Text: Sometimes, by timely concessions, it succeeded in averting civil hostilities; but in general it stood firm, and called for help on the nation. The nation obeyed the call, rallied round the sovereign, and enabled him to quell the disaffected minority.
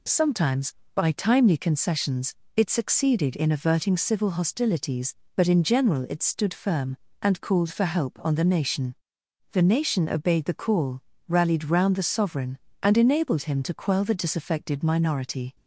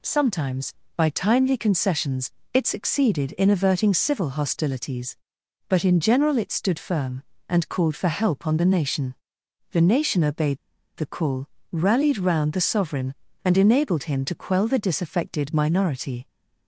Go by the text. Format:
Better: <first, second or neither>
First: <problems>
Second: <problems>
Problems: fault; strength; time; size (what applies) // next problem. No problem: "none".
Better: first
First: none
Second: pauses between "obeyed" and "the"; at 10.5 s; 0.39 s long